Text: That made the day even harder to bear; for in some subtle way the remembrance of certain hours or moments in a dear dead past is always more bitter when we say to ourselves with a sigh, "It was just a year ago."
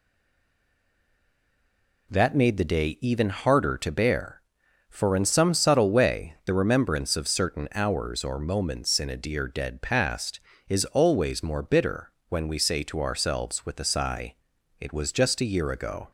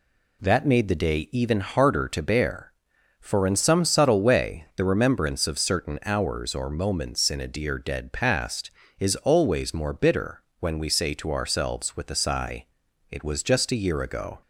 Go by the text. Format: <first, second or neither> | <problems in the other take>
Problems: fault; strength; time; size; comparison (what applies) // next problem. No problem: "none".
second | stays silent before the first word; noticeable; until 2.1 s; 2.1 s long // pauses between "bitter" and "when"; slight; at 12.1 s; 0.16 s long; slight in the second